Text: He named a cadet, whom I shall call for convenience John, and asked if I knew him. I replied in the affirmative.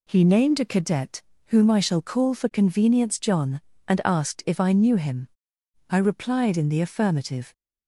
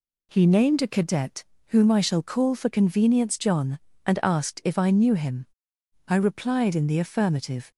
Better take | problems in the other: neither | none

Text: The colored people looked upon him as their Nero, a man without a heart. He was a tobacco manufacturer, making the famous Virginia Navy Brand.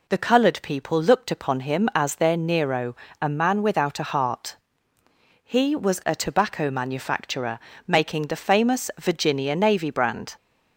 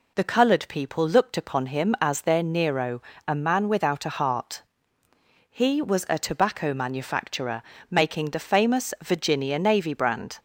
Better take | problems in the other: neither | none

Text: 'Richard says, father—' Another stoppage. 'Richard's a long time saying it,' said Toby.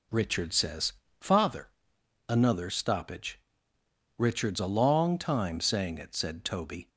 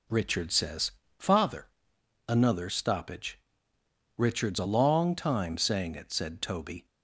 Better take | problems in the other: neither | none

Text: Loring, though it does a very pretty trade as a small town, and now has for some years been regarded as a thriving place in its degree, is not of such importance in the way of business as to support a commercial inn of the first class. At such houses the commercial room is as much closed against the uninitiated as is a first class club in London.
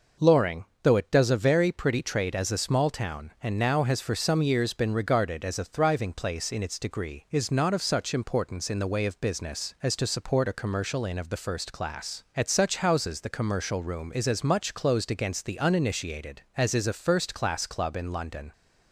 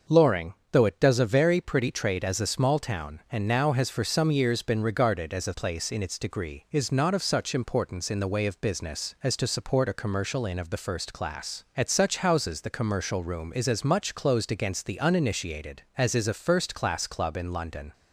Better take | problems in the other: first | starts louder than the rest; noticeable; until 1.2 s; 6 dB // skips "thriving"; at 5.5 s

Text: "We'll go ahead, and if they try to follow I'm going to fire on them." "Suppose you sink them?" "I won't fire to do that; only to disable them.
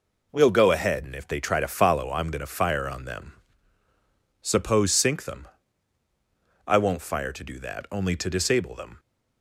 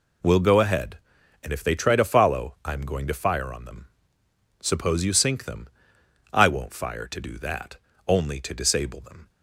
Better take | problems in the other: second | skips "you"; at 4.9 s

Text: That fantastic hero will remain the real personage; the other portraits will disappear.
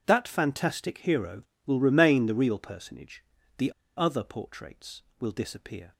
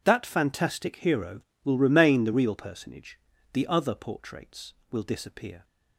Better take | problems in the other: second | pauses between "the" and "other"; slight; at 3.7 s; 0.26 s long

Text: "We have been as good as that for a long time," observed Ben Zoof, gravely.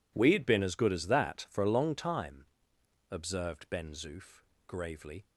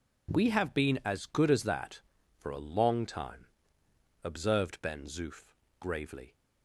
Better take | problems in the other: second | says "had" for "have"; at 0.3 s

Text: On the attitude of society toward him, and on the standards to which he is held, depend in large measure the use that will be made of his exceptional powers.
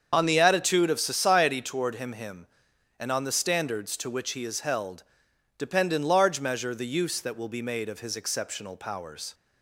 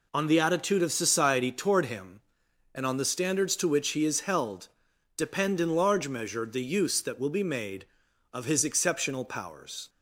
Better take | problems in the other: second | starts louder than the rest; until 1.1 s; 7 dB // says "him" twice; at 2.1 s

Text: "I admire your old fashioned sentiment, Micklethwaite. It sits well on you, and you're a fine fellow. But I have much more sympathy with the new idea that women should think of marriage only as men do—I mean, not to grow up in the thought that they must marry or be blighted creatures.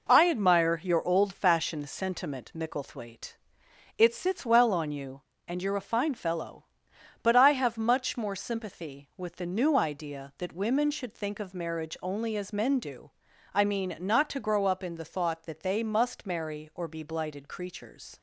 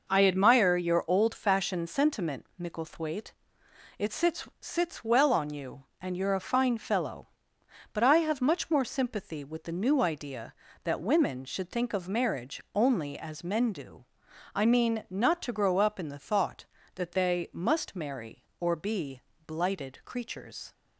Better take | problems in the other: first | says "sits" twice; at 4.5 s // pauses between "be" and "blighted"; slight; at 19.1 s; 0.26 s long

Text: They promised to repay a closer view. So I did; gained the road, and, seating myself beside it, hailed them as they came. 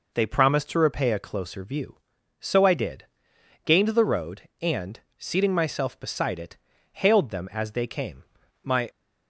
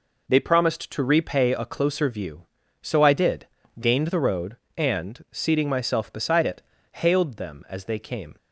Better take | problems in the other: second | goes on to say "My"; slight; from 8.6 s on; 0.28 s long

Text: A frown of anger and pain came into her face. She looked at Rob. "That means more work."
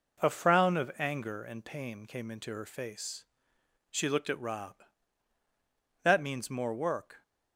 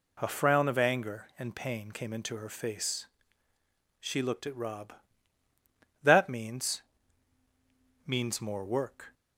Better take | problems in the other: first | says "means" twice; at 8.0 s

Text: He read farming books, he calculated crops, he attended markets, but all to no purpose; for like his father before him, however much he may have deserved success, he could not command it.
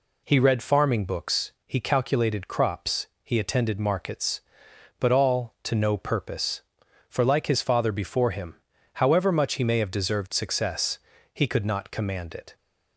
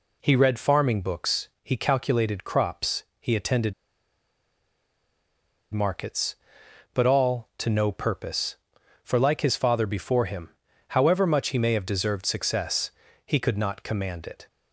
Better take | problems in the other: first | pauses between "attended" and "markets"; strong; at 3.7 s; 1.9 s long

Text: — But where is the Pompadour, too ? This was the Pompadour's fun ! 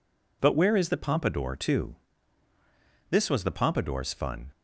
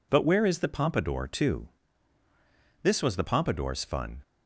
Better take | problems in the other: neither | none

